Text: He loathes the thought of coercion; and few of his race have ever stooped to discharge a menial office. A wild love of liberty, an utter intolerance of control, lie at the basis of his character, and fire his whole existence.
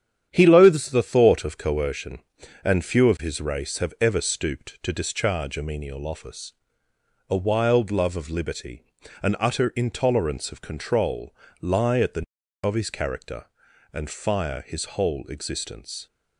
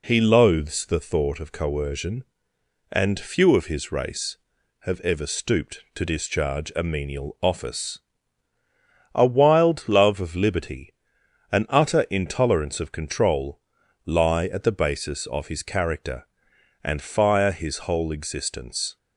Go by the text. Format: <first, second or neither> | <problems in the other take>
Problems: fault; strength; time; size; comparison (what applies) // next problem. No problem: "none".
second | starts louder than the rest; strong; until 1.3 s; 9.5 dB // skips "basis"; at 12.4 s